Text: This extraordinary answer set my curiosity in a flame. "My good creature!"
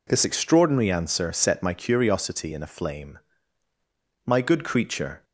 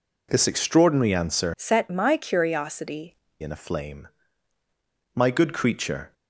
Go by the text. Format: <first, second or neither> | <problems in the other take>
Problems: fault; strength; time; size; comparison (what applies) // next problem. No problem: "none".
first | changes voice from "set" to "curiosity"; from 1.5 to 3.1 s; 1.6 s long